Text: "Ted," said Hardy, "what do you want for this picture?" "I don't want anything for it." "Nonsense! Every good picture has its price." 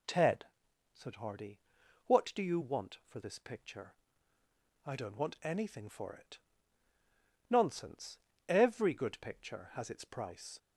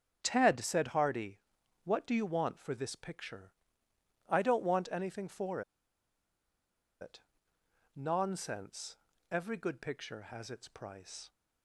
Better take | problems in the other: first | starts louder than the rest; strong; until 1.2 s; 7.5 dB // pauses between "for" and "it"; strong; at 5.6 s; 1.3 s long

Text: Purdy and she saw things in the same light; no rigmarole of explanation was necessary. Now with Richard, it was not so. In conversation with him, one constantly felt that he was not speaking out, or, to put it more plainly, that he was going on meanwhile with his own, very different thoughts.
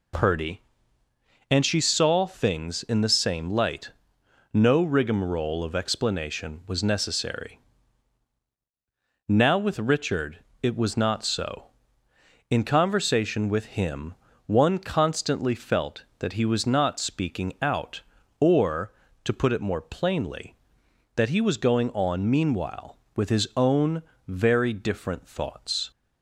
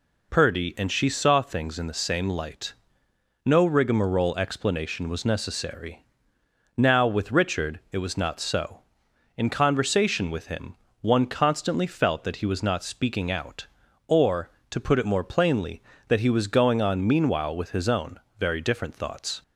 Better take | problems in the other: first | skips "of"; at 4.3 s

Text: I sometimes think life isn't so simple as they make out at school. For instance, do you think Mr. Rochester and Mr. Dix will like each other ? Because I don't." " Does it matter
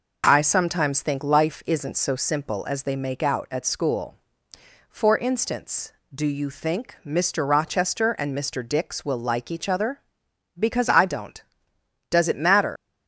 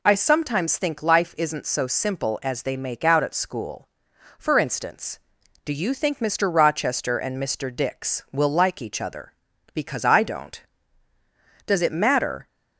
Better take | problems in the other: second | leaves "matter" unfinished; at 12.7 s; 90 ms

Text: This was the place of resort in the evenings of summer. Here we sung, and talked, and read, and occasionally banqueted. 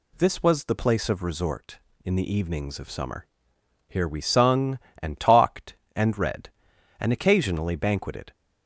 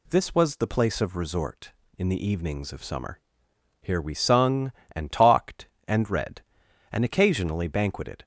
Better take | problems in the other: neither | none

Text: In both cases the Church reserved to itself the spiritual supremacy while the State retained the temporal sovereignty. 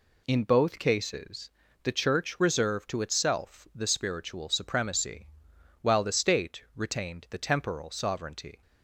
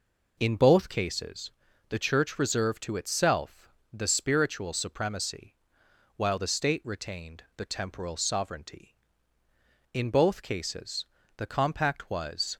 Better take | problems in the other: first | pauses between "cases" and "the"; at 1.5 s; 0.38 s long; slight in the first // pauses between "itself" and "the"; slight; at 3.6 s; 0.24 s long // pauses between "supremacy" and "while"; noticeable; at 5.5 s; 0.58 s long; noticeable in the first // goes on to say "In both cases the compact was"; strong; from 9.9 s on; 2.6 s long

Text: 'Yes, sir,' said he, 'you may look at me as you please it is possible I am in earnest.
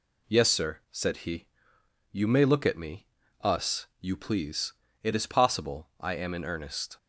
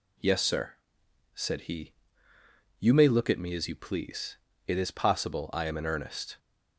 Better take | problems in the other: second | says "us" for "as"; at 3.4 s // pauses between "please" and "it"; slight; at 4.7 s; 0.30 s long; slight in the second

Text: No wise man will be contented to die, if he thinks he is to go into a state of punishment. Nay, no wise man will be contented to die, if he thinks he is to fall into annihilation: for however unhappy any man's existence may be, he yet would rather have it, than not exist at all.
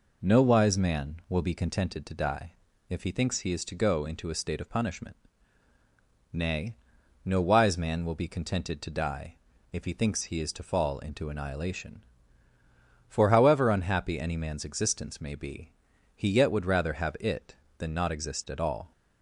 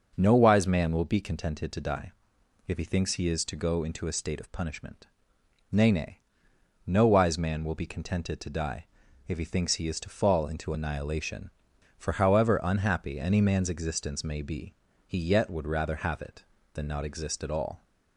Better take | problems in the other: first | says "Nay" twice; at 5.8 s

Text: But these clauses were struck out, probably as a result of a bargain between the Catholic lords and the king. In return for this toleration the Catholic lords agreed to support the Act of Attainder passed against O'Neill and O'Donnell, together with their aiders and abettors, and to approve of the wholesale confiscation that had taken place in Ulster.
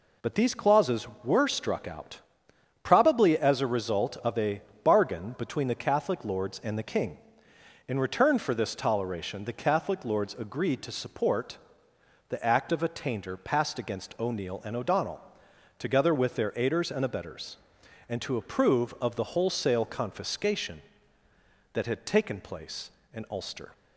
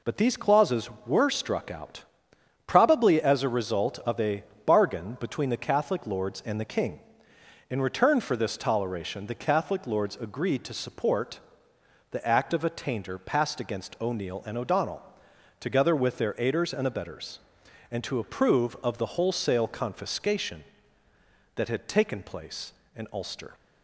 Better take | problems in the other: neither | pauses between "a" and "bargain"; slight; the same in both // pauses between "support" and "the"; noticeable; the same in both

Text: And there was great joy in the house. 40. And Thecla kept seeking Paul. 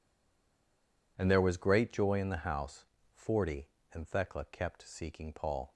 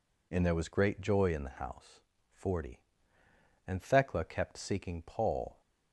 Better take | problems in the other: second | stays silent before the first word; until 1.1 s; 1.1 s long

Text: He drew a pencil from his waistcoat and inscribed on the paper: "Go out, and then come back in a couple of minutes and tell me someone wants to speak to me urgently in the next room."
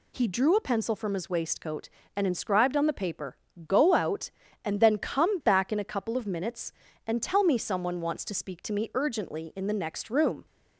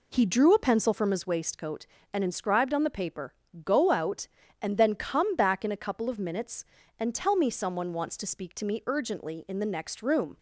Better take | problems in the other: first | starts louder than the rest; slight; until 1.4 s; 3 dB

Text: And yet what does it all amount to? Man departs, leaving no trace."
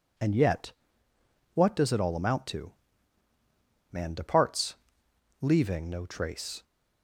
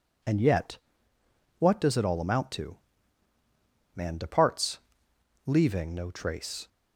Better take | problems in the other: neither | pauses between "yet" and "what"; noticeable; the same in both

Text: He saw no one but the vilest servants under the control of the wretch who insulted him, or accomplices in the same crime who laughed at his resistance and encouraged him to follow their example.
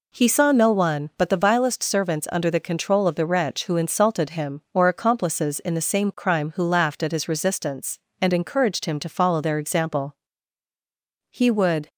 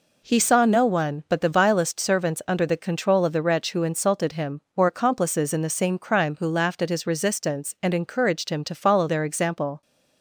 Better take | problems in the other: second | goes on to say "He would"; from 11.3 s on; 0.58 s long

